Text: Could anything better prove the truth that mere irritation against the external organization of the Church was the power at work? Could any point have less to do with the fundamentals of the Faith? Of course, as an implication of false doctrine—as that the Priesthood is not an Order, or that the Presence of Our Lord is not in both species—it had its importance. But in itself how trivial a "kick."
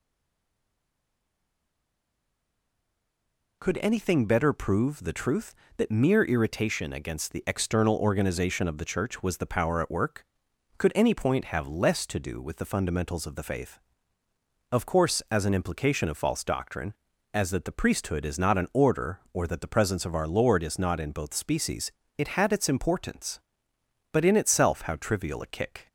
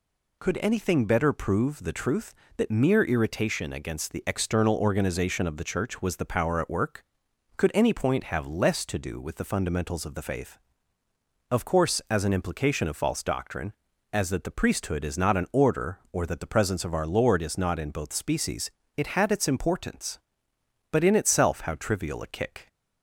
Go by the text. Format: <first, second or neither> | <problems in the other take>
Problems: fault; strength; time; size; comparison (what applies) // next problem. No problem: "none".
second | stays silent before the first word; strong; until 3.6 s; 3.6 s long